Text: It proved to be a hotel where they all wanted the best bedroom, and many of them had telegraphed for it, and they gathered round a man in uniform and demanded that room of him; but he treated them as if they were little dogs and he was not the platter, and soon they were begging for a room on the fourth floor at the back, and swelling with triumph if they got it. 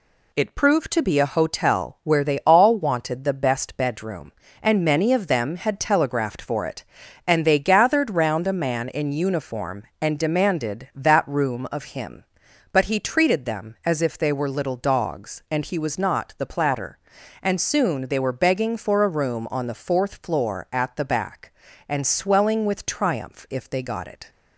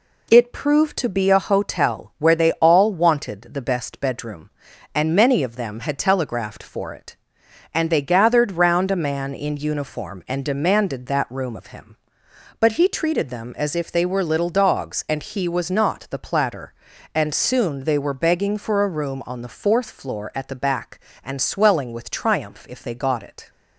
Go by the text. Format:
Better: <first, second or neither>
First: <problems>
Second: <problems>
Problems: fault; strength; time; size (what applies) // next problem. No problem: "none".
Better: neither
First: none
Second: none